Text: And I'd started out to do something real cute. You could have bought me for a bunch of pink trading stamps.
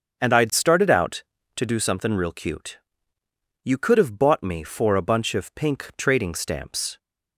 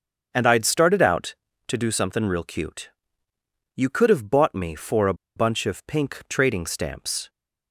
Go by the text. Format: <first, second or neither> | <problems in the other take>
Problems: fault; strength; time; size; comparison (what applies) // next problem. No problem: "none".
first | starts louder than the rest; until 1.3 s; 7 dB; also in the first // pauses between "a" and "bunch"; slight; at 5.1 s; 0.22 s long